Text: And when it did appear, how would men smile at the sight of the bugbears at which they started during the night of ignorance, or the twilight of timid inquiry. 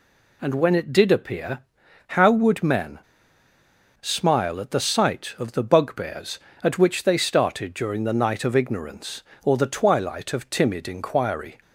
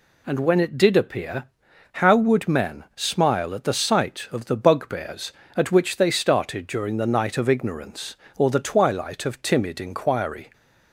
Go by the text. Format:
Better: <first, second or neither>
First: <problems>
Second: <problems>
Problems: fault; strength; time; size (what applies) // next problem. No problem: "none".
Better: second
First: pauses between "men" and "smile"; at 2.9 s; 1.0 s long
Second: none